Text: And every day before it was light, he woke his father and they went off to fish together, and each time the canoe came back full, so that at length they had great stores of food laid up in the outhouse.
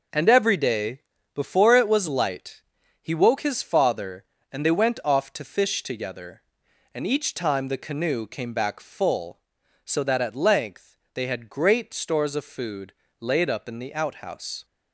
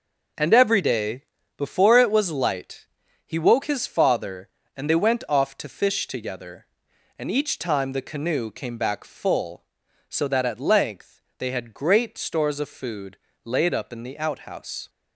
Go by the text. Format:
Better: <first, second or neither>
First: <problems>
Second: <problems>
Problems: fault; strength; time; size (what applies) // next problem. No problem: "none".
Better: neither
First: pauses between "day" and "before"; slight; at 1.0 s; 0.34 s long // pauses between "length" and "they"; slight; at 10.9 s; 0.16 s long // pauses between "food" and "laid"; slight; at 12.9 s; 0.28 s long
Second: pauses between "day" and "before"; slight; at 1.2 s; 0.34 s long // pauses between "length" and "they"; slight; at 11.2 s; 0.16 s long // pauses between "food" and "laid"; slight; at 13.1 s; 0.28 s long